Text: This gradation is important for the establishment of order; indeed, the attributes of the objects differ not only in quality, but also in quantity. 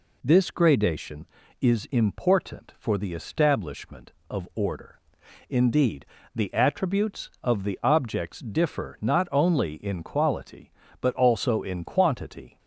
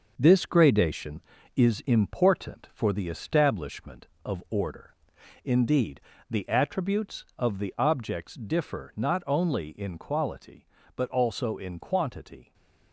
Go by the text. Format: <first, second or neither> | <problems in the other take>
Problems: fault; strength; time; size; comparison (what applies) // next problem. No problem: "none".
first | gets quieter; noticeable; throughout; 6 dB